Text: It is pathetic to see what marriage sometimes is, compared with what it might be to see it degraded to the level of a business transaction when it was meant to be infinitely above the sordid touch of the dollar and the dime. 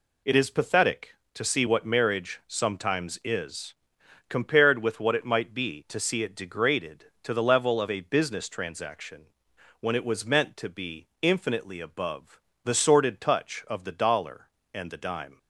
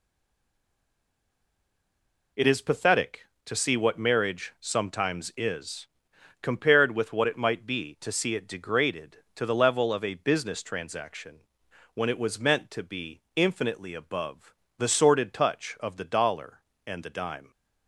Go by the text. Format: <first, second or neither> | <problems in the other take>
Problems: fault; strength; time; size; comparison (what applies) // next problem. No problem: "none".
first | stays silent before the first word; until 2.3 s; 2.3 s long // pauses between "transaction" and "when"; noticeable; at 11.3 s; 0.56 s long; noticeable in the first // pauses between "above" and "the"; slight; at 14.5 s; 0.24 s long; slight in the first